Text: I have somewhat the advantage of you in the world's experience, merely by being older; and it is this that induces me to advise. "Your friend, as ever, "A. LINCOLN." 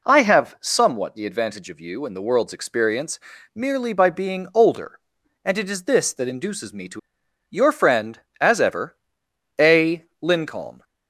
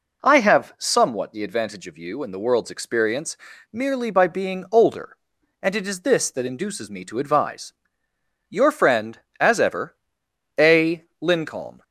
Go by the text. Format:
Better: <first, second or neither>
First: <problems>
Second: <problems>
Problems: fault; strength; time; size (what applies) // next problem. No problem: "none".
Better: second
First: skips "advise"; at 7.2 s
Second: none